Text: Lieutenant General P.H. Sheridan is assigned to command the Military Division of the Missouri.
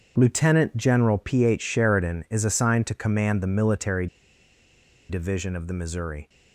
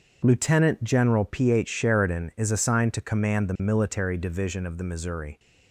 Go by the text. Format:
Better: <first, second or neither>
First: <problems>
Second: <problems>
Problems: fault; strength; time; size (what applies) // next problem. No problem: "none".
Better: second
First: starts louder than the rest; until 1.1 s; 7 dB // pauses between "Military" and "Division"; at 4.0 s; 1.0 s long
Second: starts louder than the rest; until 1.2 s; 7 dB